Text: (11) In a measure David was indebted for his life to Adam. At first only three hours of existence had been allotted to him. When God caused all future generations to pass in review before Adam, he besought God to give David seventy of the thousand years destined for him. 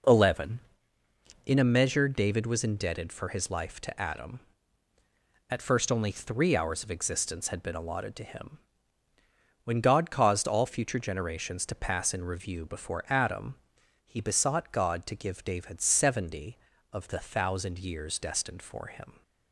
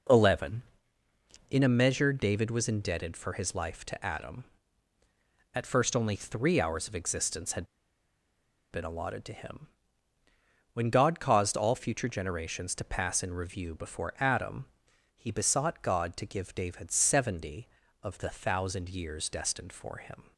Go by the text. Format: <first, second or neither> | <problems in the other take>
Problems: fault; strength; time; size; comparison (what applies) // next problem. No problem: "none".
first | pauses between "had" and "been"; at 7.6 s; 1.0 s long